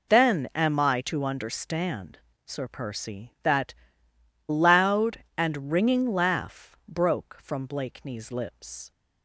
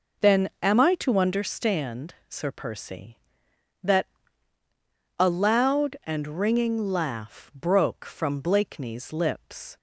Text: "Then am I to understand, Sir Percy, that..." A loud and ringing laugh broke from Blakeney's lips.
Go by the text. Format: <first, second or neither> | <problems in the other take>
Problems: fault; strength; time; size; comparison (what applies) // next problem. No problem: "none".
second | skips "A"; at 4.1 s